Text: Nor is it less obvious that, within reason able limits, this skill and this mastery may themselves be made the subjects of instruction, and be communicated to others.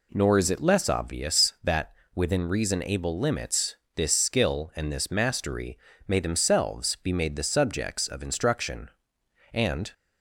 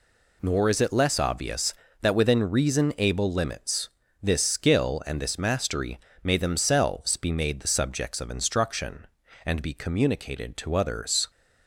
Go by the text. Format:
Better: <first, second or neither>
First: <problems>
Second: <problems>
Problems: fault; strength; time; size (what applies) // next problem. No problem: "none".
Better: second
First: pauses between "mastery" and "may"; slight; at 5.7 s; 0.30 s long // stops before "be communicated to others"; at 9.9 s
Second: pauses between "mastery" and "may"; slight; at 5.9 s; 0.26 s long